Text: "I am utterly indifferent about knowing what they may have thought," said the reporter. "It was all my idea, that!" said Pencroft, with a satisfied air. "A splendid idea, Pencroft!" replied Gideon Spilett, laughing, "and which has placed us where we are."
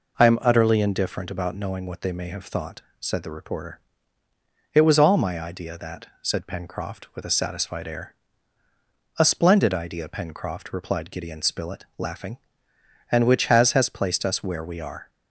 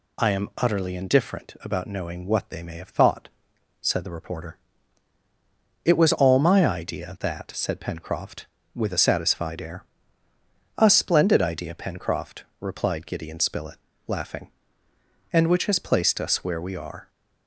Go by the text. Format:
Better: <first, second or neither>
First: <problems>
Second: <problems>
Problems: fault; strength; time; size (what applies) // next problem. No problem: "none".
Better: second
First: says "has" twice; at 13.7 s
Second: none